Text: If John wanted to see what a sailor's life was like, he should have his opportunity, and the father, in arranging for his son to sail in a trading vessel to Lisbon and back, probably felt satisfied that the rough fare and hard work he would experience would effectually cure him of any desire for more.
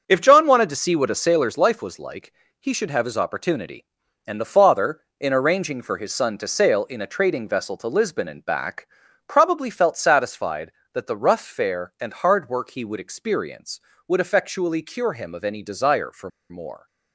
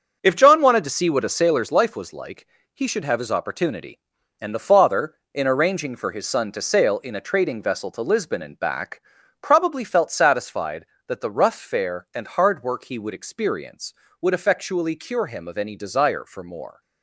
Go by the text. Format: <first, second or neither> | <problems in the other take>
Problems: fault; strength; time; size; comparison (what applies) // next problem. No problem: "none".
second | starts louder than the rest; until 1.0 s; 6 dB; also in the second // pauses between "for" and "more"; slight; at 16.2 s; 0.21 s long